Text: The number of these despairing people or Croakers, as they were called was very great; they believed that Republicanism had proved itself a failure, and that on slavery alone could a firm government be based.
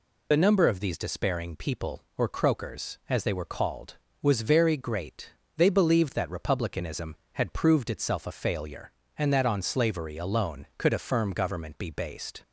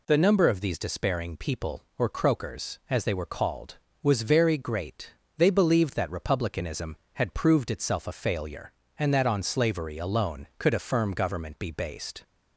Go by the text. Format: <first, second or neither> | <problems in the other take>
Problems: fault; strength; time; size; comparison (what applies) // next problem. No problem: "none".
second | loses the start of "The"; at 0.3 s; 45 ms